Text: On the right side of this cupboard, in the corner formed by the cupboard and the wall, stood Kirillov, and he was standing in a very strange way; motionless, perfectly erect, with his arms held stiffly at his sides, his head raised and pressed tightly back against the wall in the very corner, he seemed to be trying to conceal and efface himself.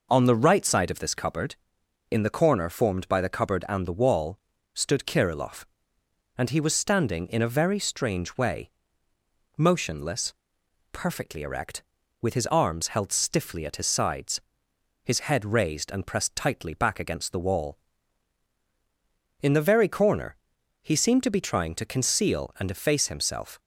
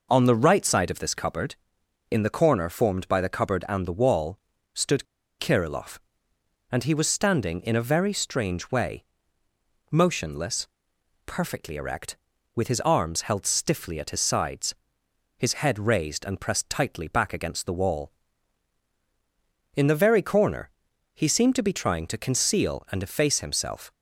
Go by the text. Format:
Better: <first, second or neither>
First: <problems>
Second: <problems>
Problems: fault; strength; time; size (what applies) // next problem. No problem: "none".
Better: first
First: none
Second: pauses between "stood" and "Kirillov"; slight; at 5.0 s; 0.34 s long